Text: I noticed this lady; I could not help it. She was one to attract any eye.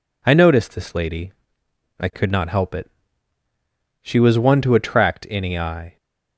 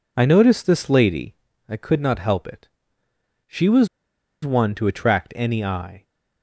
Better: first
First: none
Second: pauses between "was" and "one"; noticeable; at 3.8 s; 0.57 s long

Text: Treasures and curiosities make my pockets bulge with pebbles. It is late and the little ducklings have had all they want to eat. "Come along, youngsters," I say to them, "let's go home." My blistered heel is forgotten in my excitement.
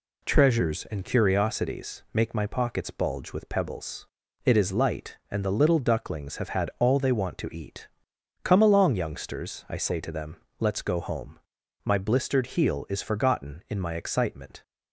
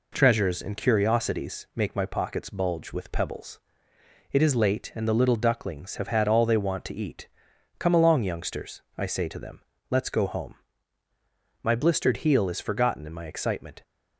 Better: second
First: says "light" for "late"; at 4.7 s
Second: none

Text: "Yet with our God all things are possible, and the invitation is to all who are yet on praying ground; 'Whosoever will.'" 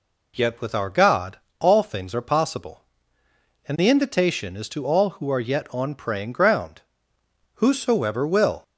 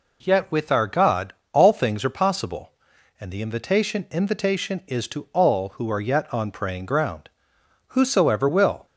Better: first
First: pauses between "God" and "all"; slight; at 1.3 s; 0.22 s long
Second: pauses between "God" and "all"; slight; at 1.3 s; 0.19 s long // says "invitation" twice; at 4.1 s

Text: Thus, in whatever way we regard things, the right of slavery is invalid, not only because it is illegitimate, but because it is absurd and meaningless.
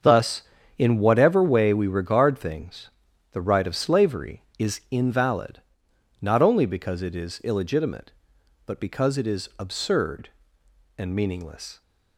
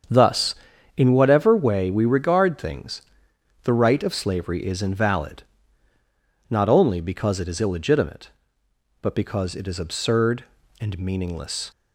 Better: neither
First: starts louder than the rest; strong; until 1.3 s; 7 dB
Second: starts louder than the rest; strong; until 1.5 s; 7.5 dB

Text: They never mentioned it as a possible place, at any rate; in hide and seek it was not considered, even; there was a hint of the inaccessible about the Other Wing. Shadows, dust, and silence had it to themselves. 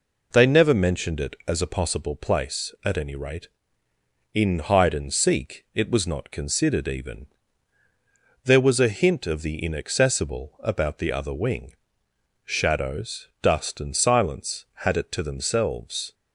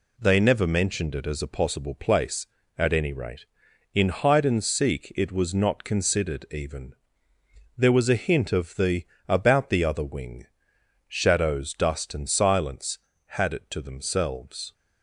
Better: first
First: none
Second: skips "inaccessible"; at 9.1 s

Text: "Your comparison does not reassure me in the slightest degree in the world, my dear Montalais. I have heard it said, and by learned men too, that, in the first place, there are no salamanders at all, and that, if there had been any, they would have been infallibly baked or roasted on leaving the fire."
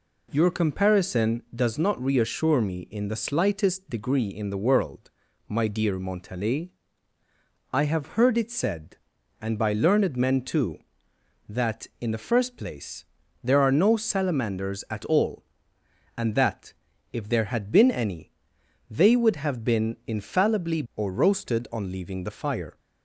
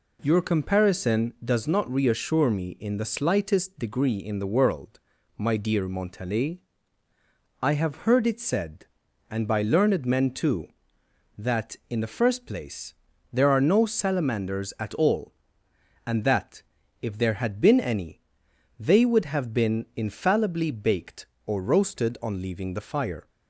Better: second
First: skips "baked"; at 20.8 s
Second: none

